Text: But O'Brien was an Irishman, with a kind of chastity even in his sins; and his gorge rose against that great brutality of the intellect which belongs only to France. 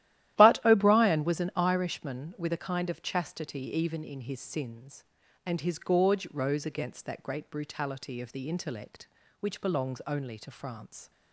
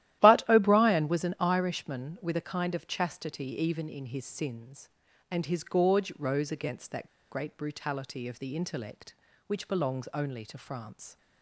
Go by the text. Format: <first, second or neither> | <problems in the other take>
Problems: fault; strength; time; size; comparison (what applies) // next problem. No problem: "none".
first | starts louder than the rest; strong; until 1.2 s; 13.5 dB; strong in the first // pauses between "that" and "great"; slight; at 7.0 s; 0.21 s long